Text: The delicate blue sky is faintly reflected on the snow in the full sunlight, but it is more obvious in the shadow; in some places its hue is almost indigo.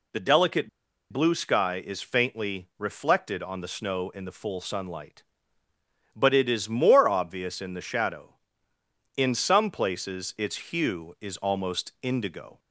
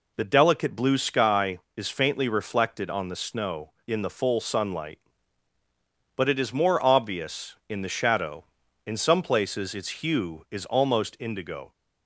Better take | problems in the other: second | pauses between "delicate" and "blue"; at 0.6 s; 0.43 s long

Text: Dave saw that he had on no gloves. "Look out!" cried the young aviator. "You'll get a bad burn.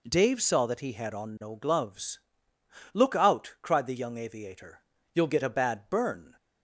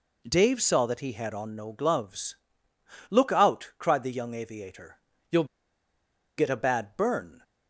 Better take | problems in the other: first | pauses between "You'll" and "get"; noticeable; at 5.4 s; 0.93 s long

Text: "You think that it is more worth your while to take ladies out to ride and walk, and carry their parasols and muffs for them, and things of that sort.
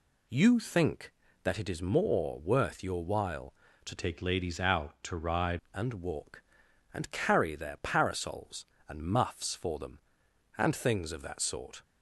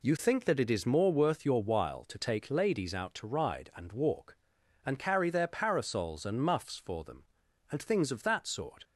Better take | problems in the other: second | changes voice from "take" to "ride"; from 3.9 to 5.5 s; 1.6 s long

